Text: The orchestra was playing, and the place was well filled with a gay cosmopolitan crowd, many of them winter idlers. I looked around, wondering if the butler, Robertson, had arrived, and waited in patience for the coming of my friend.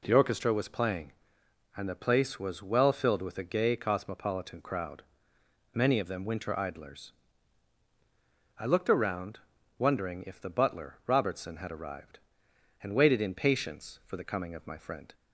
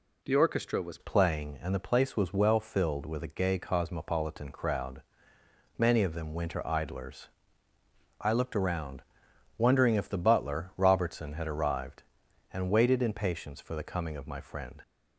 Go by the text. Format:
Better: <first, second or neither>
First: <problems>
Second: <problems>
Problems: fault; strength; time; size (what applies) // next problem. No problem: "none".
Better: first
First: none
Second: changes voice at "playing"; from 0.9 s on; 13.9 s long